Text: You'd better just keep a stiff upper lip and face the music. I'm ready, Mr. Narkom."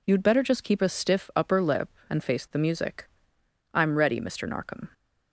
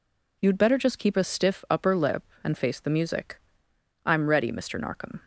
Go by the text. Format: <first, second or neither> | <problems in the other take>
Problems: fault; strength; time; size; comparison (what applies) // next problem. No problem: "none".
neither | none